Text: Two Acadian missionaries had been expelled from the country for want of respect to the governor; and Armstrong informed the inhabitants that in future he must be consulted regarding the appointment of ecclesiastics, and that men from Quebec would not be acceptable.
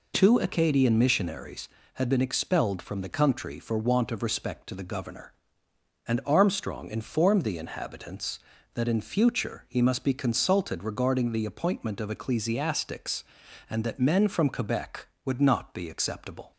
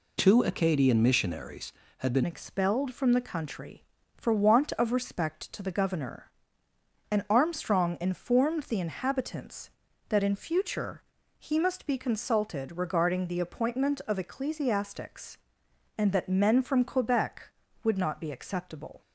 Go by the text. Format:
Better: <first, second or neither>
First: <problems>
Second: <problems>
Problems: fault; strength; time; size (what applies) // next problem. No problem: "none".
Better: first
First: none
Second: changes voice at "expelled"; from 2.2 s on; 16.8 s long // pauses between "future" and "he"; slight; at 11.0 s; 0.34 s long